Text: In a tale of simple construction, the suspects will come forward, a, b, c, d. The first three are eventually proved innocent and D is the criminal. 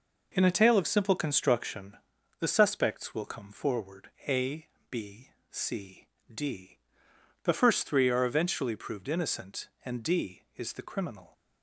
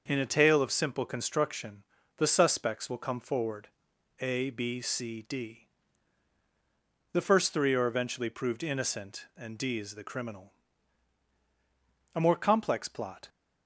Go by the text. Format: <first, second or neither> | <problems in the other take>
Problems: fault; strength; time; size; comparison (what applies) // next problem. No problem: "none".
first | starts louder than the rest; noticeable; until 1.0 s; 6 dB // goes on to say "A more complex plot"; noticeable; from 12.1 s on; 1.1 s long